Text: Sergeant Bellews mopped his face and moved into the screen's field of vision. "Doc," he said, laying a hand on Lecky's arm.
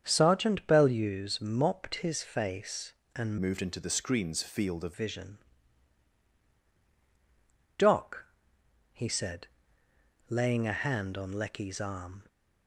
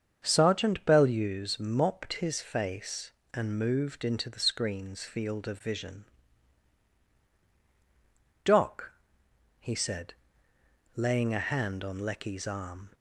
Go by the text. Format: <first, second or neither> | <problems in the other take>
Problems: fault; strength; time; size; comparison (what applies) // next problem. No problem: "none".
second | starts louder than the rest; strong; until 1.0 s; 7.5 dB; strong in the second // changes voice from "moved" to "of"; from 3.4 to 4.9 s; 1.5 s long